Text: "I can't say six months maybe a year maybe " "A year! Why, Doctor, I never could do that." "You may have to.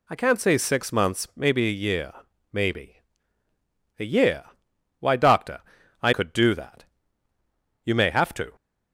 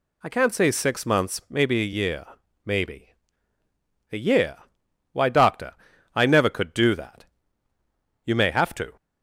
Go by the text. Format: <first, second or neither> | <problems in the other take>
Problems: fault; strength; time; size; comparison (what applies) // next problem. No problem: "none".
second | pauses between "year" and "maybe"; at 2.1 s; 0.40 s long; also in the second // skips "never"; at 6.1 s